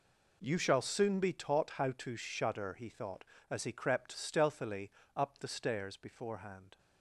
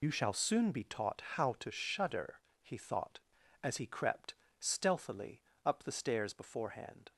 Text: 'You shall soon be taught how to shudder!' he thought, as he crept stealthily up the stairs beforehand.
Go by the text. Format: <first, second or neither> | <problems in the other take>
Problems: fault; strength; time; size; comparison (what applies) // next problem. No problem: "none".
first | loses the start of "You"; at 0.0 s; 70 ms // pauses between "crept" and "stealthily"; slight; at 4.3 s; 0.24 s long // pauses between "stealthily" and "up"; slight; at 5.4 s; 0.22 s long; slight in the first